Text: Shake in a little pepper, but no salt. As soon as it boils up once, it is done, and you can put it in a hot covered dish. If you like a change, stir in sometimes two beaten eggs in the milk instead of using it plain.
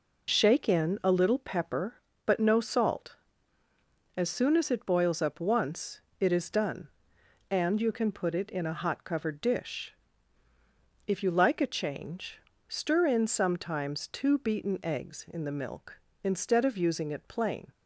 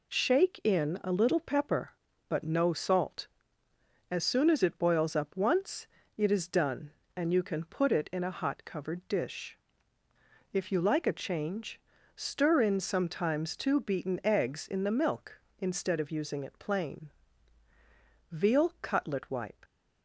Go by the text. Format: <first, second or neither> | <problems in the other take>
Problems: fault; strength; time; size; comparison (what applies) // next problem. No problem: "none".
first | goes on to say "Veal Cutlet Wipe"; from 18.3 s on; 1.3 s long